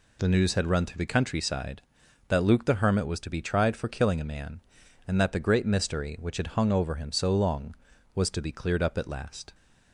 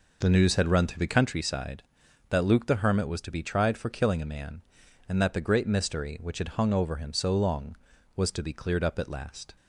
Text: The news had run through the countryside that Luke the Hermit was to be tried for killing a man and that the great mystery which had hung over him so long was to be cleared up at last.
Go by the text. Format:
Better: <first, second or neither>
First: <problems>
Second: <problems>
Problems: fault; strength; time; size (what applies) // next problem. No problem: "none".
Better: first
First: none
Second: starts louder than the rest; noticeable; until 1.3 s; 5 dB